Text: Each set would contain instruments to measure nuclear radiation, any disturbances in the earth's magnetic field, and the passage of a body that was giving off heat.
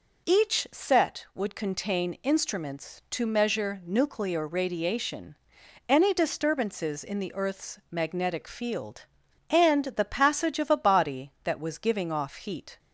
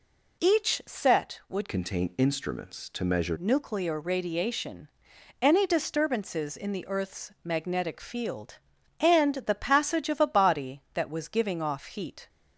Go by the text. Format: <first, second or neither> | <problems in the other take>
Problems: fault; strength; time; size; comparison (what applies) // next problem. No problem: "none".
first | changes voice from "contain" to "measure"; from 1.6 to 3.3 s; 1.7 s long